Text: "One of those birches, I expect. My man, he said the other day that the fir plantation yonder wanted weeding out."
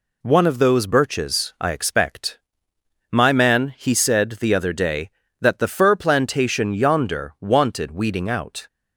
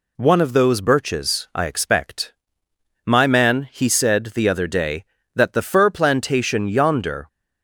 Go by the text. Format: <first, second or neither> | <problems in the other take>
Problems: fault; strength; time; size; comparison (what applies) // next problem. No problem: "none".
first | stops before "wanted weeding out"; at 7.2 s